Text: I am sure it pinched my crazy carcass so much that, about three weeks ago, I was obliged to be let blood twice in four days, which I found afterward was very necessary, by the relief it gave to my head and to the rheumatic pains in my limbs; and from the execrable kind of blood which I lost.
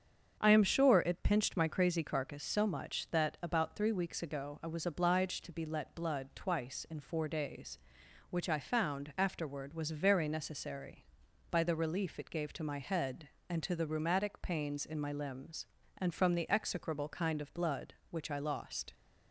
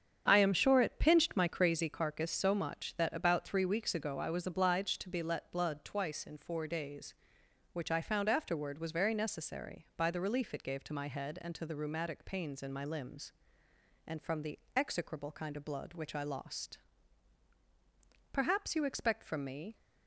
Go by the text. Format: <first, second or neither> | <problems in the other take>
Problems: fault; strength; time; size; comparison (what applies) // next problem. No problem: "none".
first | starts louder than the rest; strong; until 1.2 s; 8 dB; strong in the first // pauses between "the" and "execrable"; slight; at 14.5 s; 0.16 s long // goes on to say "Perhaps you expect from me"; from 18.3 s on; 1.4 s long